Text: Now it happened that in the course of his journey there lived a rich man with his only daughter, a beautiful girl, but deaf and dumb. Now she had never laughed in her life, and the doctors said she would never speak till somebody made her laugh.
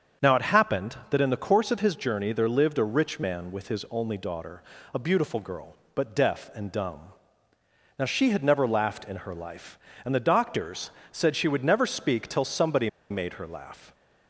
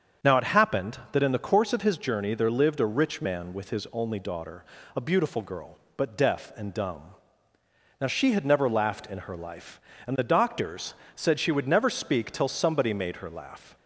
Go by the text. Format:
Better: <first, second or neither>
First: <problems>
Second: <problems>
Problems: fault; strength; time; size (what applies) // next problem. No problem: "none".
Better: second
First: starts louder than the rest; strong; until 1.3 s; 7 dB // pauses between "doctors" and "said"; slight; at 10.9 s; 0.20 s long // pauses between "somebody" and "made"; slight; at 12.8 s; 0.21 s long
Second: starts louder than the rest; strong; until 1.3 s; 7 dB // pauses between "doctors" and "said"; slight; at 10.9 s; 0.20 s long